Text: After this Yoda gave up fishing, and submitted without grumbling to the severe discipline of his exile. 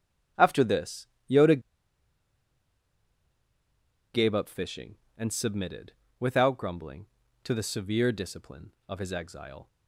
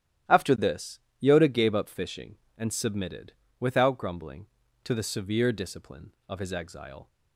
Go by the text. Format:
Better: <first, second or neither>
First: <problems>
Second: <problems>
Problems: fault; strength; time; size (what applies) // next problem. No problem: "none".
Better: second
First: starts louder than the rest; strong; until 1.6 s; 12 dB // pauses between "this" and "Yoda"; slight; at 1.0 s; 0.22 s long // pauses between "Yoda" and "gave"; strong; at 1.5 s; 2.5 s long // pauses between "submitted" and "without"; slight; at 5.9 s; 0.28 s long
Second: starts louder than the rest; strong; until 1.5 s; 12 dB // pauses between "this" and "Yoda"; slight; at 0.9 s; 0.22 s long // pauses between "submitted" and "without"; slight; at 3.3 s; 0.28 s long